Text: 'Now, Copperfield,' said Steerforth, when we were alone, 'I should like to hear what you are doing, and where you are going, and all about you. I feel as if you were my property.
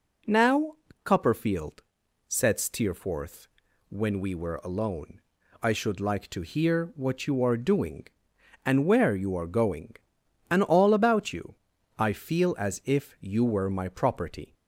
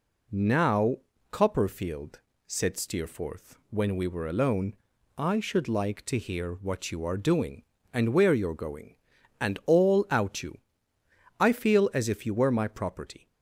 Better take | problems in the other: first | says "out" for "about"; at 10.1 s

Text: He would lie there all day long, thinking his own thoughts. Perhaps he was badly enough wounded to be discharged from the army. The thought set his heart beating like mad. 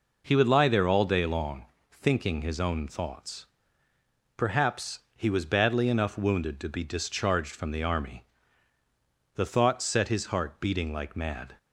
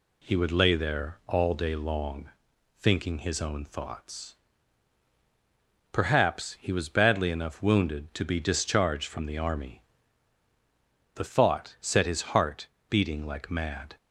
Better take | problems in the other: first | says "lay" for "lie"; at 0.5 s // pauses between "heart" and "beating"; slight; at 12.6 s; 0.22 s long

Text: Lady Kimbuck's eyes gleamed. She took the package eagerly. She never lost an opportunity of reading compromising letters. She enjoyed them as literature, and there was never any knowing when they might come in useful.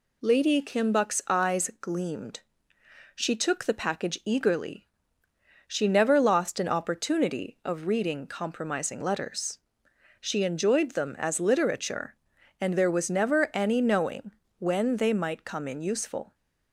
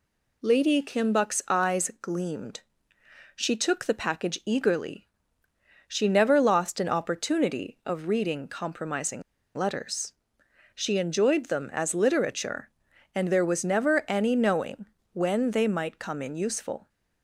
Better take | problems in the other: first | pauses between "compromising" and "letters"; slight; at 9.2 s; 0.34 s long // pauses between "knowing" and "when"; slight; at 14.8 s; 0.30 s long; slight in the first

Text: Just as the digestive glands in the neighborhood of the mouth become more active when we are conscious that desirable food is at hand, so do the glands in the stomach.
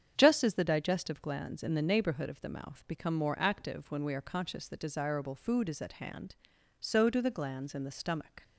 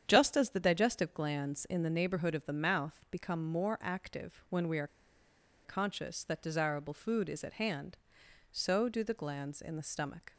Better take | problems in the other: first | starts louder than the rest; strong; until 1.0 s; 8.5 dB; strong in the first // pauses between "are" and "conscious"; noticeable; at 4.8 s; 0.77 s long

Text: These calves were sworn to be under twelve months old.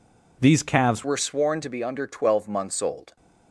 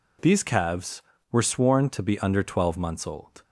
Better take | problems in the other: second | changes voice at "were"; from 1.0 s on; 2.1 s long

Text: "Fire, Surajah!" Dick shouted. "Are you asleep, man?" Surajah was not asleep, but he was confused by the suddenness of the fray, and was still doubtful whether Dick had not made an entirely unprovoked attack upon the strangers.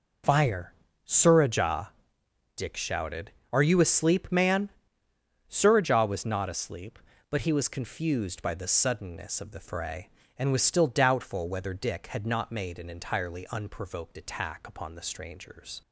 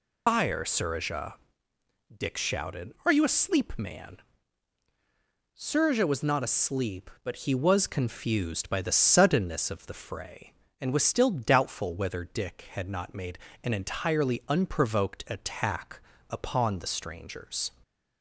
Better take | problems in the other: first | loses the start of "Fire"; at 0.2 s; 90 ms // pauses between "made" and "an"; slight; at 13.3 s; 0.26 s long // pauses between "attack" and "upon"; slight; at 16.0 s; 0.30 s long

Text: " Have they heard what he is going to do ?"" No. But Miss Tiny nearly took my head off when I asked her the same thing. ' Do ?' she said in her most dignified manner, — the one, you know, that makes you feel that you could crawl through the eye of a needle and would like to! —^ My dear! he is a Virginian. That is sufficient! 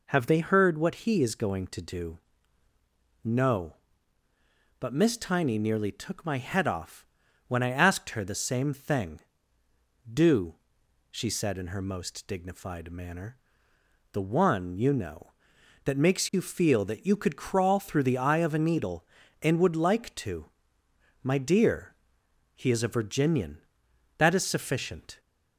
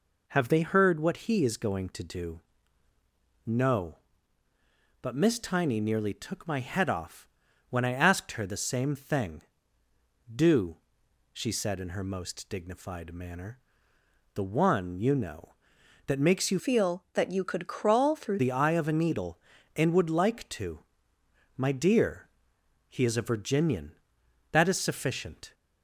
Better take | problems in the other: first | pauses between "off" and "when"; at 7.2 s; 0.40 s long; also in the first // changes voice from "feel" to "through"; from 16.5 to 18.4 s; 1.9 s long

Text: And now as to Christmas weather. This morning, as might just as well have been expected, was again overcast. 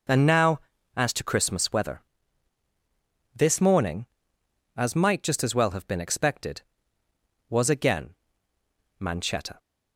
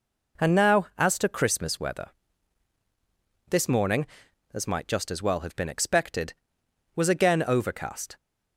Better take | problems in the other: second | says "manchetta" for "overcast"; at 8.9 s

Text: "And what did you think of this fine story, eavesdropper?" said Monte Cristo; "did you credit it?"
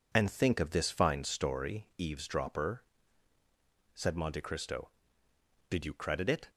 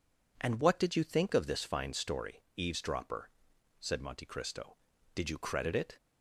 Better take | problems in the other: second | skips "what did you"; at 0.2 s

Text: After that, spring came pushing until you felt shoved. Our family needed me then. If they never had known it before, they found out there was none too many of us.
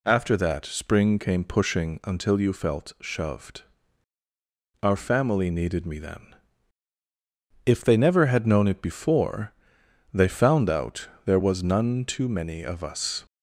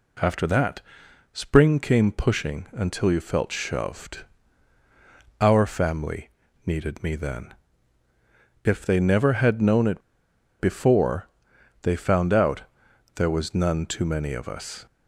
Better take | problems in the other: first | pauses between "family" and "needed"; slight; at 6.2 s; 0.36 s long // pauses between "it" and "before"; noticeable; at 10.0 s; 0.58 s long // pauses between "out" and "there"; noticeable; at 12.6 s; 0.54 s long; slight in the first

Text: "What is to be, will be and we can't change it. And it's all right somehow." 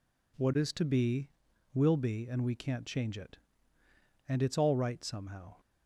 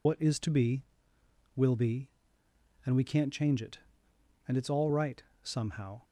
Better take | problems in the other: first | loses the start of "What"; at 0.0 s; 70 ms // pauses between "right" and "somehow"; slight; at 5.2 s; 0.22 s long

